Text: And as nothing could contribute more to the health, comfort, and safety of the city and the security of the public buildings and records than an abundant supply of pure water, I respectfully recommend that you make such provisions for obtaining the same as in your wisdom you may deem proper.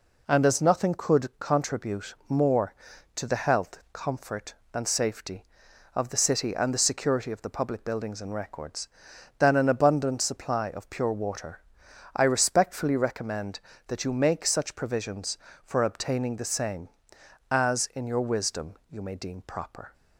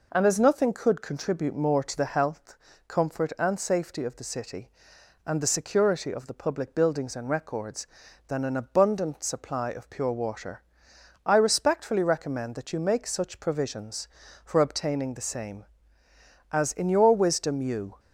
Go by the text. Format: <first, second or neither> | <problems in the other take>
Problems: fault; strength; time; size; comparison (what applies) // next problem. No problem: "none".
first | stops before "may deem proper"; at 17.9 s